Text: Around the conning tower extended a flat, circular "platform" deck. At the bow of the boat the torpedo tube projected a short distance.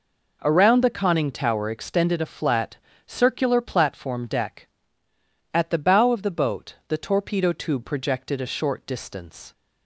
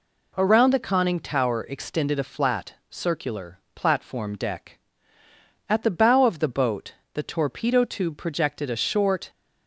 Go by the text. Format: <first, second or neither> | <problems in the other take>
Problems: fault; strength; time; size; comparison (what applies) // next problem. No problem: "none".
first | pauses between "circular" and "platform"; slight; at 3.5 s; 0.16 s long // pauses between "boat" and "the"; slight; at 6.9 s; 0.20 s long // stops before "distance"; at 9.2 s